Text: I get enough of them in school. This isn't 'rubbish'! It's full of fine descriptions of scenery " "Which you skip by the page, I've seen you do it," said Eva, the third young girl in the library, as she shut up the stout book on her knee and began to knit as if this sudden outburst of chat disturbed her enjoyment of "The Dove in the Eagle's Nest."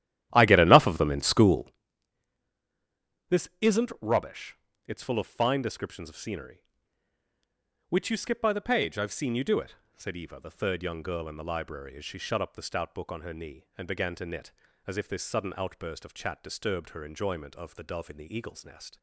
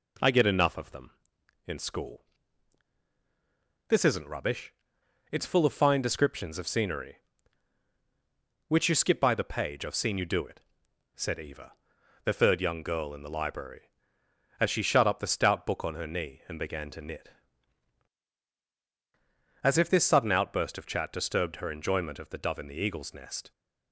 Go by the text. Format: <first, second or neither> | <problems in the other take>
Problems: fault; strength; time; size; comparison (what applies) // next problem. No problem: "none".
second | starts louder than the rest; strong; until 1.8 s; 13 dB